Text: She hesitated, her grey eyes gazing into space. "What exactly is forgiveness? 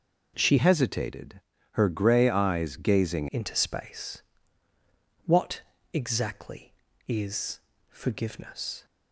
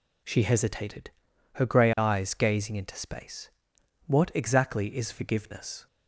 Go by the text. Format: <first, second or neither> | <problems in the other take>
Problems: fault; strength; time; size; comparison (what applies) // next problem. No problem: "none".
second | changes voice from "hesitated" to "gazing"; from 0.5 to 3.2 s; 2.7 s long // pauses between "What" and "exactly"; slight; at 5.6 s; 0.32 s long // pauses between "is" and "forgiveness"; slight; at 7.5 s; 0.32 s long